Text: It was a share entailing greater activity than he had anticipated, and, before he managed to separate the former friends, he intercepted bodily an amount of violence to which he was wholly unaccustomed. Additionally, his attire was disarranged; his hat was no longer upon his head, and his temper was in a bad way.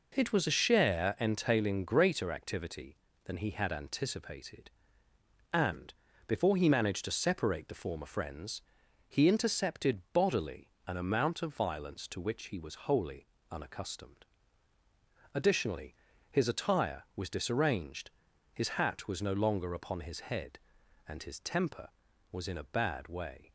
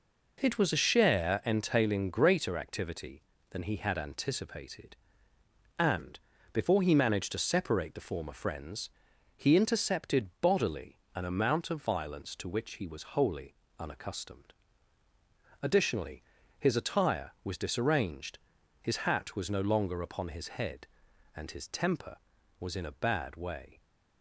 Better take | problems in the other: neither | pauses between "bodily" and "an"; slight; the same in both // pauses between "wholly" and "unaccustomed"; slight; the same in both

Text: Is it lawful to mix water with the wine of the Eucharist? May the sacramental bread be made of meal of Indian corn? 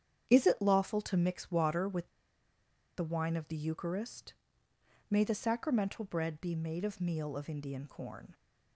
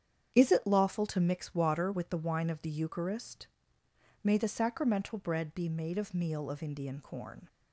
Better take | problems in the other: second | starts louder than the rest; strong; until 1.3 s; 8.5 dB; strong in the second // pauses between "with" and "the"; noticeable; at 2.0 s; 0.89 s long

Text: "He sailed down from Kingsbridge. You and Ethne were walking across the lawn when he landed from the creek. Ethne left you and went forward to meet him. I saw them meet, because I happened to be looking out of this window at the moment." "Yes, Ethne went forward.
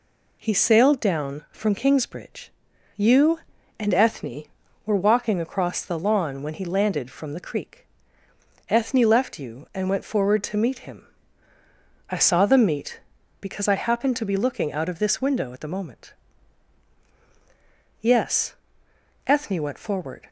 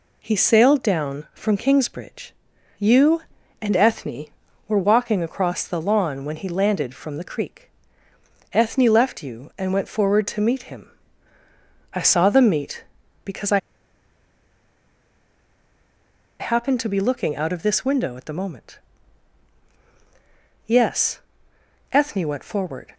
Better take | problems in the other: first | pauses between "I" and "happened"; strong; at 13.5 s; 2.8 s long

